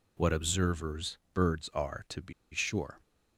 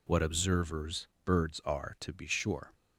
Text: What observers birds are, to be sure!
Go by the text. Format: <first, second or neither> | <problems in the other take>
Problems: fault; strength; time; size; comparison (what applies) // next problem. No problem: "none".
second | pauses between "observers" and "birds"; slight; at 1.1 s; 0.16 s long; slight in the second // pauses between "be" and "sure"; slight; at 2.3 s; 0.19 s long